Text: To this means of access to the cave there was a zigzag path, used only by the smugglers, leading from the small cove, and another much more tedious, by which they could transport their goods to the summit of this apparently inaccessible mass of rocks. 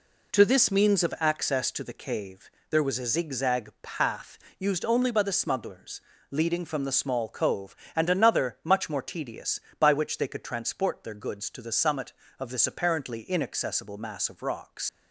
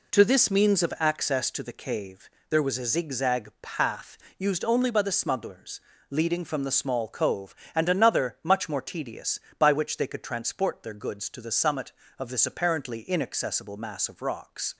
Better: second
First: pauses between "cave" and "there"; slight; at 2.5 s; 0.18 s long // leaves "rocks" unfinished; at 14.8 s; 80 ms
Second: pauses between "cave" and "there"; slight; at 2.3 s; 0.18 s long

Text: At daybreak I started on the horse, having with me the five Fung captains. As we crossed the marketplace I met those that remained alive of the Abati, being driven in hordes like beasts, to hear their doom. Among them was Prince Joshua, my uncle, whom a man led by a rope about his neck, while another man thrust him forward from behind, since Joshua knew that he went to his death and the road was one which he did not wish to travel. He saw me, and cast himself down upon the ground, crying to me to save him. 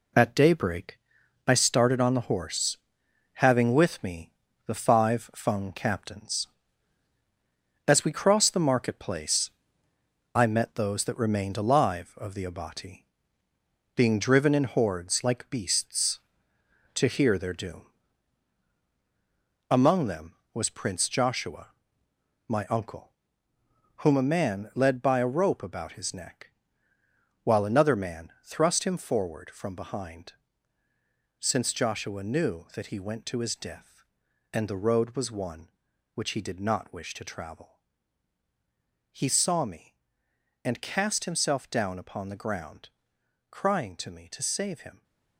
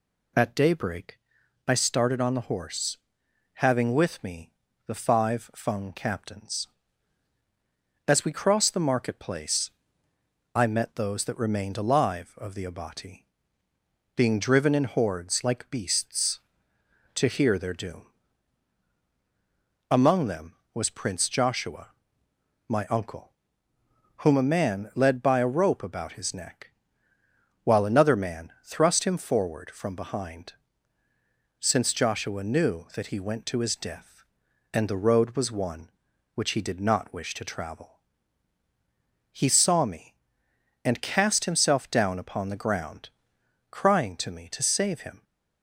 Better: second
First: gets quieter; throughout; 7 dB // pauses between "daybreak" and "I"; noticeable; at 0.9 s; 0.48 s long // pauses between "me" and "the"; slight; at 4.3 s; 0.36 s long // pauses between "marketplace" and "I"; noticeable; at 9.4 s; 0.86 s long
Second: pauses between "daybreak" and "I"; noticeable; at 1.1 s; 0.48 s long // pauses between "me" and "the"; slight; at 4.5 s; 0.36 s long // pauses between "marketplace" and "I"; noticeable; at 9.6 s; 0.86 s long

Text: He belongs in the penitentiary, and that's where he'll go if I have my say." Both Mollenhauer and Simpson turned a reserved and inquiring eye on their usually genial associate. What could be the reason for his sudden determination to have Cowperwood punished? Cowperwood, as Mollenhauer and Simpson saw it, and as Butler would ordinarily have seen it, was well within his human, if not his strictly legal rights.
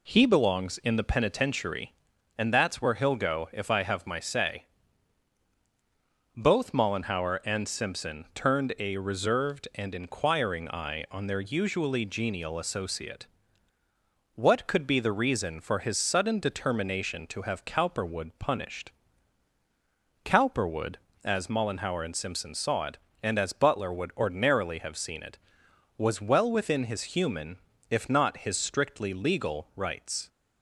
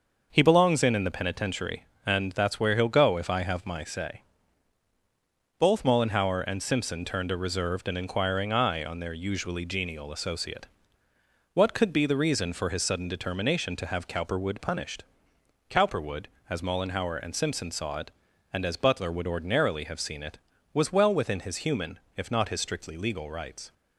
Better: first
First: none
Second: starts louder than the rest; noticeable; until 1.3 s; 6 dB // says "in" twice; at 0.9 s

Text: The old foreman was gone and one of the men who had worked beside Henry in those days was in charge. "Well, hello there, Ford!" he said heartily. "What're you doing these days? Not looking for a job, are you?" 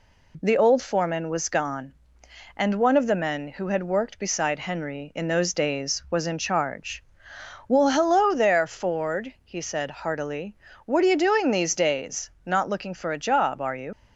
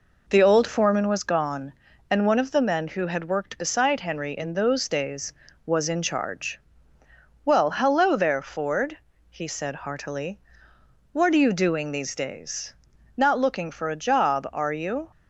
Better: second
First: leaves "you" unfinished; at 13.9 s; 50 ms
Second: none

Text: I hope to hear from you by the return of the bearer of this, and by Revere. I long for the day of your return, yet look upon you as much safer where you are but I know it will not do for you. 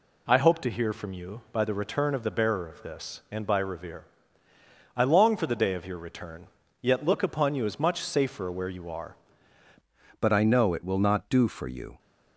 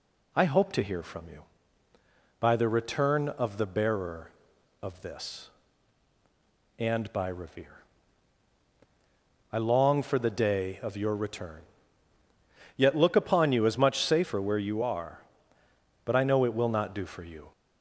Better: second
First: changes voice at "but"; from 10.1 s on; 1.8 s long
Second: none

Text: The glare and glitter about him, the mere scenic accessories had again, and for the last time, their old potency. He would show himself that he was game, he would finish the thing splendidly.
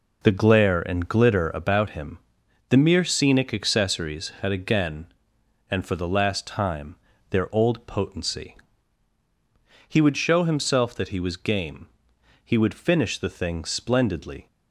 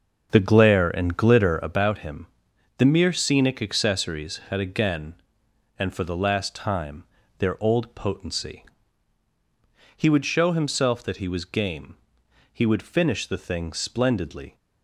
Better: first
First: none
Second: starts louder than the rest; until 1.9 s; 6.5 dB

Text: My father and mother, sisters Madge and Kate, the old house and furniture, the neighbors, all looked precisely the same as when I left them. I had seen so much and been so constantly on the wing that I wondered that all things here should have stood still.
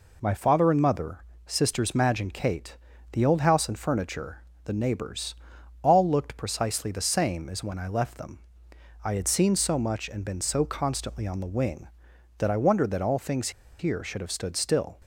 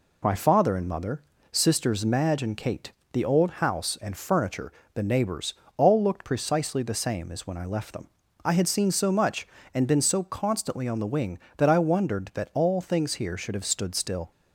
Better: second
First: pauses between "things" and "here"; slight; at 13.4 s; 0.29 s long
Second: none

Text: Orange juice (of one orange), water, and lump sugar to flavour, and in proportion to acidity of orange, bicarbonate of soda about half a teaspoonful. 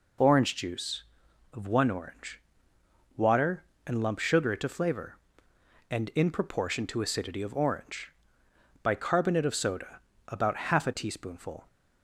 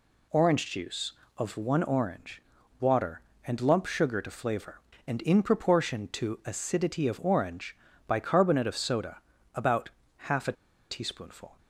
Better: first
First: pauses between "soda" and "about"; slight; at 10.0 s; 0.26 s long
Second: pauses between "soda" and "about"; slight; at 9.2 s; 0.32 s long // pauses between "about" and "half"; at 9.8 s; 0.38 s long // pauses between "a" and "teaspoonful"; at 10.5 s; 0.38 s long

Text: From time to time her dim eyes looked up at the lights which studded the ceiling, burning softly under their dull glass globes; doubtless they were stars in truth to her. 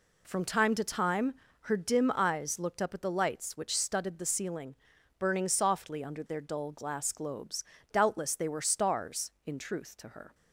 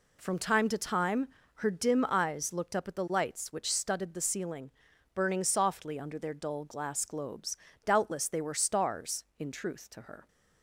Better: neither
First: pauses between "time" and "her"; slight; at 1.3 s; 0.28 s long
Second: pauses between "time" and "her"; slight; at 1.2 s; 0.28 s long

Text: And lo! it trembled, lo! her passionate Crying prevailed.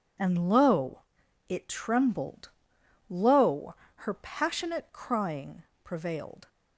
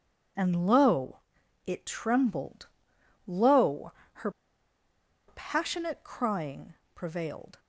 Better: first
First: pauses between "Crying" and "prevailed"; slight; at 5.6 s; 0.20 s long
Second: pauses between "her" and "passionate"; noticeable; at 4.3 s; 0.96 s long // pauses between "Crying" and "prevailed"; slight; at 6.7 s; 0.20 s long

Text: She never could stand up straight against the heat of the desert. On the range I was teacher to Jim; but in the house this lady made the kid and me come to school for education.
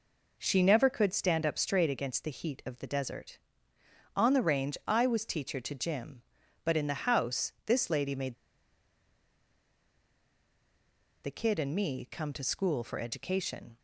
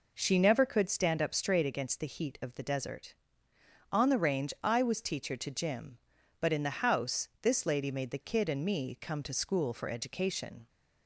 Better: second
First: pauses between "made" and "the"; strong; at 8.3 s; 2.8 s long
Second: none

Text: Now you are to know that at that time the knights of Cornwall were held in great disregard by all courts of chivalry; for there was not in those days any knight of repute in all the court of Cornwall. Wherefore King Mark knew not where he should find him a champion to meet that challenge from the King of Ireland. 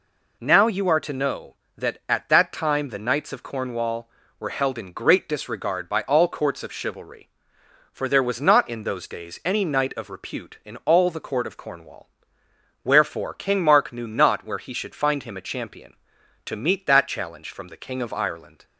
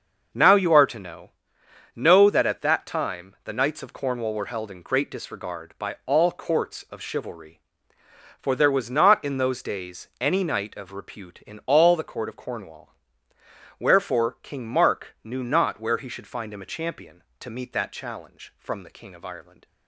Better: first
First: none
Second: starts louder than the rest; noticeable; until 1.9 s; 6 dB // says "know" twice; at 1.9 s

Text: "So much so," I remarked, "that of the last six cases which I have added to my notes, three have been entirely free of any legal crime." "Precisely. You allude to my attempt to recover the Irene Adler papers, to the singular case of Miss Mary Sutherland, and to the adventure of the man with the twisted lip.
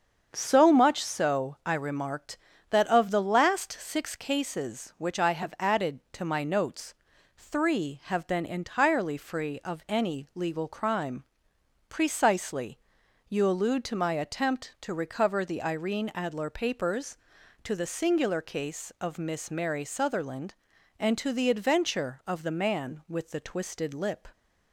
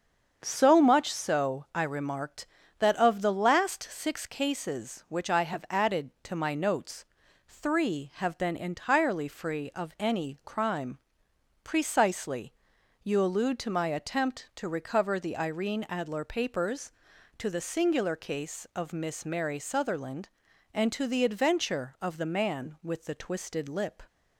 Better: first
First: starts louder than the rest; strong; until 1.3 s; 7 dB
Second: starts louder than the rest; strong; until 1.4 s; 7 dB // skips "legal"; at 10.4 s

